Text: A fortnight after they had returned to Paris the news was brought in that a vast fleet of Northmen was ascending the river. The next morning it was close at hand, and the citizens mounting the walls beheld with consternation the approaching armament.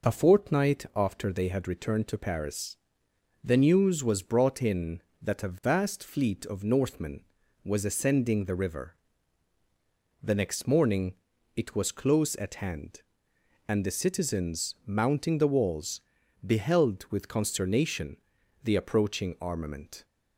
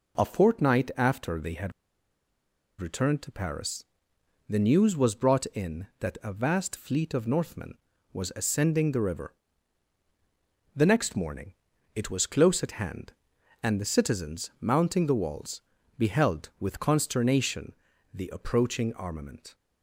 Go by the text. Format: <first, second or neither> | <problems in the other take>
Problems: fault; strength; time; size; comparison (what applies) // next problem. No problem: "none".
first | pauses between "had" and "returned"; at 1.7 s; 1.0 s long // pauses between "Paris" and "the"; noticeable; at 3.8 s; 0.64 s long; noticeable in the first // pauses between "morning" and "it"; at 11.5 s; 0.42 s long; also in the first // pauses between "walls" and "beheld"; slight; at 15.6 s; 0.36 s long; also in the first // pauses between "consternation" and "the"; at 17.7 s; 0.40 s long; noticeable in the first